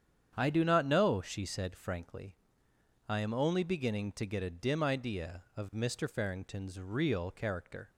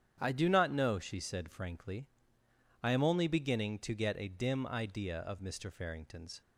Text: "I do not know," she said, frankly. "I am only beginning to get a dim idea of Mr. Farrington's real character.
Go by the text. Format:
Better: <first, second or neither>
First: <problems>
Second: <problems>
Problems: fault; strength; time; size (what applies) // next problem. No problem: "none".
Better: first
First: starts louder than the rest; strong; until 1.3 s; 8.5 dB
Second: starts louder than the rest; strong; until 1.2 s; 9 dB // stops before "real character"; at 6.4 s